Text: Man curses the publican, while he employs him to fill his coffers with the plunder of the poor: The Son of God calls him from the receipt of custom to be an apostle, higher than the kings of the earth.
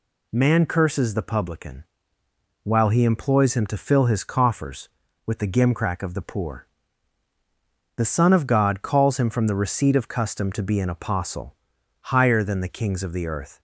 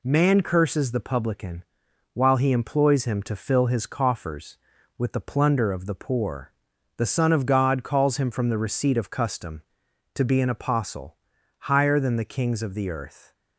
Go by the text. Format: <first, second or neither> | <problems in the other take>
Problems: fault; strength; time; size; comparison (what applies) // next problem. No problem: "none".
second | says "gimcrack" for "plunder"; at 5.4 s